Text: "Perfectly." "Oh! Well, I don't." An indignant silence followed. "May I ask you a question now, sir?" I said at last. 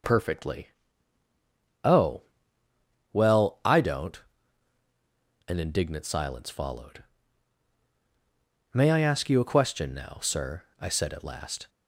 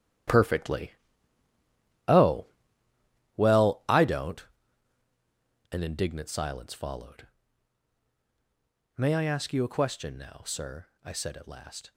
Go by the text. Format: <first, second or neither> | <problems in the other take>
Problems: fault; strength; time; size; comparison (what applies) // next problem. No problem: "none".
first | gets quieter; strong; throughout; 12 dB